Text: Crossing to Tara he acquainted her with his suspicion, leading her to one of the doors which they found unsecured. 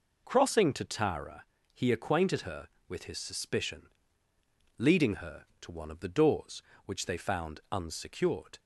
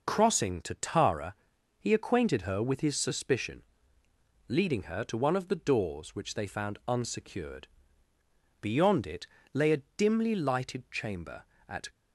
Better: first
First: pauses between "Tara" and "he"; slight; at 1.4 s; 0.28 s long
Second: pauses between "Tara" and "he"; at 1.3 s; 0.44 s long // goes on to say "Beyond it lay a dimly lighted chamber at"; strong; from 8.6 s on; 3.2 s long

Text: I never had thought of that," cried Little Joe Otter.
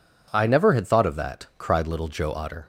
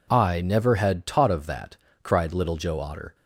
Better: first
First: none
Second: says "taught" for "thought"; at 1.0 s

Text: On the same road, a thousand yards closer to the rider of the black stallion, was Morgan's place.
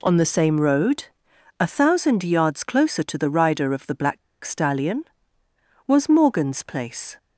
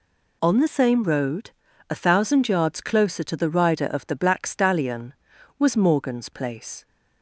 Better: second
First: pauses between "black" and "stallion"; slight; at 4.1 s; 0.25 s long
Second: none

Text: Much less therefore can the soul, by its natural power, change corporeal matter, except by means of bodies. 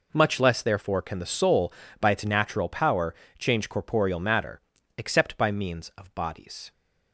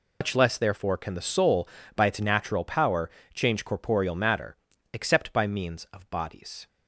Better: first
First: none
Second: loses the start of "Much"; at 0.2 s; 135 ms

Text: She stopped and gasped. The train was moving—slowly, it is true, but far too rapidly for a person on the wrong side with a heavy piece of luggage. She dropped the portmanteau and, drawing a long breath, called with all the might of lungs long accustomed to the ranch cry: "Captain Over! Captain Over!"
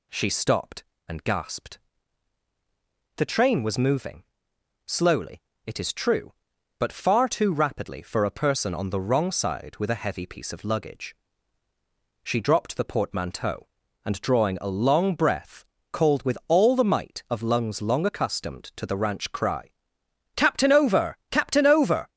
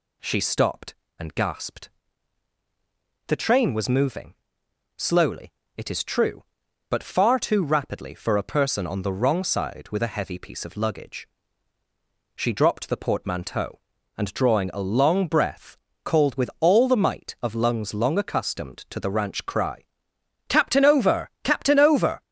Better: neither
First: none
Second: none

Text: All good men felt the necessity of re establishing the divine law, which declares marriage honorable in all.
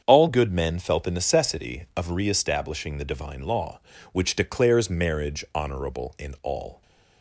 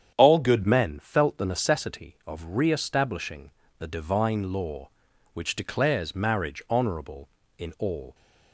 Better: first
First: starts louder than the rest; strong; until 1.0 s; 7.5 dB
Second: starts louder than the rest; strong; until 1.1 s; 8.5 dB // changes voice at "men"; from 0.6 s on; 7.5 s long // pauses between "establishing" and "the"; slight; at 3.5 s; 0.26 s long

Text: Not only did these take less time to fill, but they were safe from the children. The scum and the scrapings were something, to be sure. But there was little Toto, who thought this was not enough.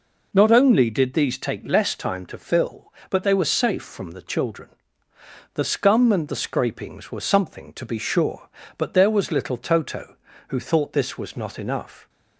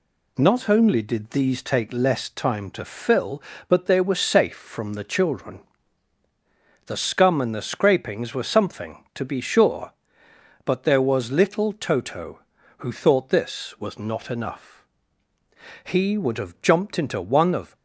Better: first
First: none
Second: goes on to say "He would have jumped into one of"; strong; from 15.8 s on; 1.9 s long

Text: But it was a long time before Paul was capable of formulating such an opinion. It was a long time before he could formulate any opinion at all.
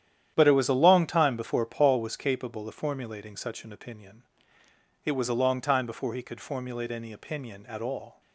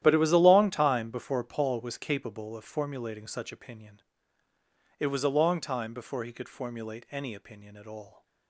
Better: first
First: starts louder than the rest; strong; until 1.3 s; 10.5 dB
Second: starts louder than the rest; strong; until 1.0 s; 12 dB // skips "an"; at 3.5 s

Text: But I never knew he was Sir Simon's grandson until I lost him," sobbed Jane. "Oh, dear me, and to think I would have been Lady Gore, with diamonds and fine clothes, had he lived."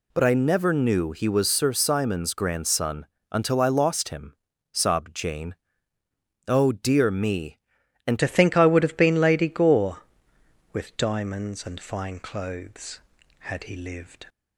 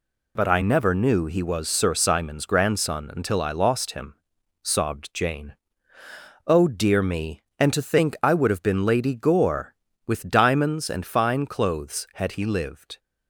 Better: second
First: pauses between "grandson" and "until"; slight; at 3.0 s; 0.24 s long // changes voice at "to"; from 8.1 s on; 6.1 s long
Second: none

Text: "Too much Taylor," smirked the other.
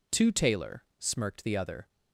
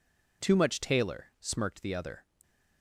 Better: second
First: skips "much"; at 0.3 s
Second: none

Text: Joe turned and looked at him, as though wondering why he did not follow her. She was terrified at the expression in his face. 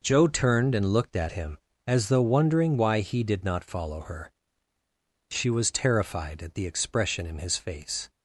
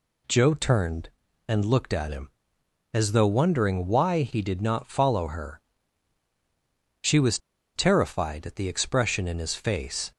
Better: first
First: none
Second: pauses between "was" and "terrified"; at 7.3 s; 0.37 s long

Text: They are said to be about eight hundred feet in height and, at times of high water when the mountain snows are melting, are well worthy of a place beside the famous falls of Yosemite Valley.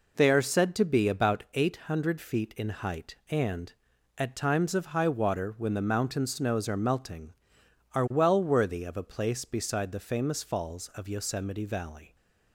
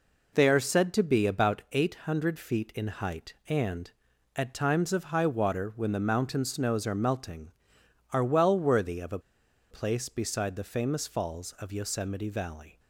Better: first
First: none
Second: pauses between "a" and "place"; noticeable; at 9.1 s; 0.51 s long

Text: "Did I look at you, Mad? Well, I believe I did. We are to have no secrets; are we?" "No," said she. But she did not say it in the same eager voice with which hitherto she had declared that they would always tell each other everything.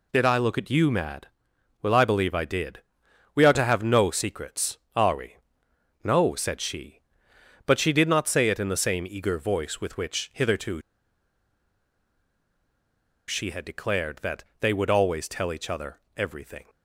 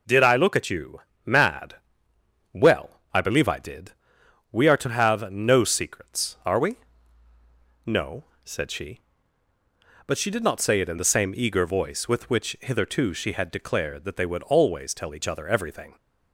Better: second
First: pauses between "hitherto" and "she"; strong; at 10.8 s; 2.4 s long // pauses between "that" and "they"; slight; at 14.4 s; 0.16 s long // pauses between "other" and "everything"; slight; at 15.9 s; 0.16 s long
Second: none

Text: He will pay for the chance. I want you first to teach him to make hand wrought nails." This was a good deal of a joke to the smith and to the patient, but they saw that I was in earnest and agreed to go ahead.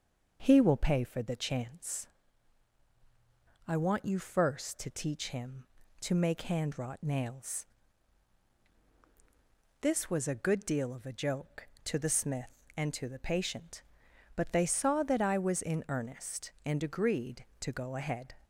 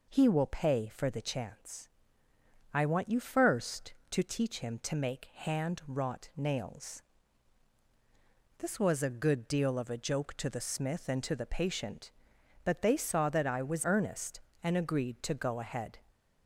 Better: first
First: none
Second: skips "in"; at 13.8 s

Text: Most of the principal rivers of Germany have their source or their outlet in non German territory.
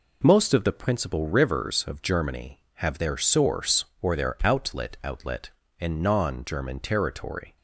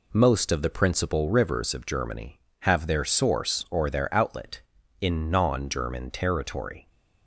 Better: second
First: says "outlet" twice; at 5.0 s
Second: none

